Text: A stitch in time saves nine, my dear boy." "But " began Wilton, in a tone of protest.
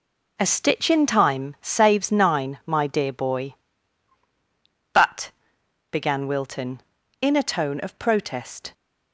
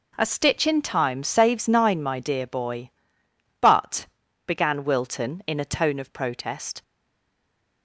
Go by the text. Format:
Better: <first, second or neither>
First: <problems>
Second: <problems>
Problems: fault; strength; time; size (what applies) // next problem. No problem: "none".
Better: first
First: none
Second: stays silent after the last word; from 6.8 s on; 1.0 s long